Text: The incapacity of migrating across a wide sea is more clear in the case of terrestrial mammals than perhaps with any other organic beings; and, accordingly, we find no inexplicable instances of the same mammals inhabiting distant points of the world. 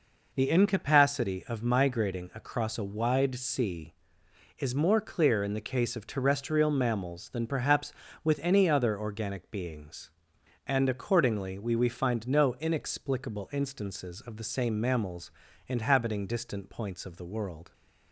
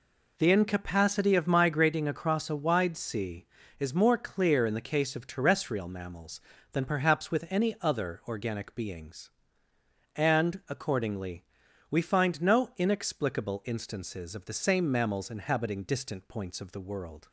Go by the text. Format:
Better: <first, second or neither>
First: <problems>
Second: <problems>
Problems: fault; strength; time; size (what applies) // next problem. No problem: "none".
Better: second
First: says "we" twice; at 11.7 s // pauses between "mammals" and "inhabiting"; slight; at 15.3 s; 0.36 s long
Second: none